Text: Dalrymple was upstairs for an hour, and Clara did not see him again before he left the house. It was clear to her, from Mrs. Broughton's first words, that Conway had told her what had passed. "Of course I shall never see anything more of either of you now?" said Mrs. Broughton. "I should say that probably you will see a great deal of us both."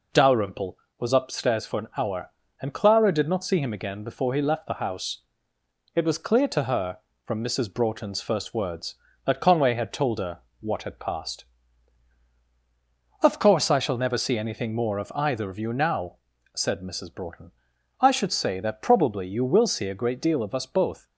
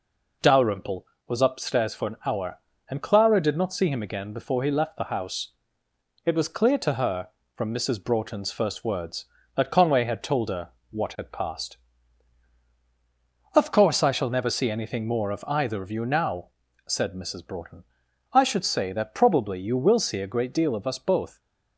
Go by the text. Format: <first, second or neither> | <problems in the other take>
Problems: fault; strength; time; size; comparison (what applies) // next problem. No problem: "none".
neither | pauses between "her" and "what"; slight; the same in both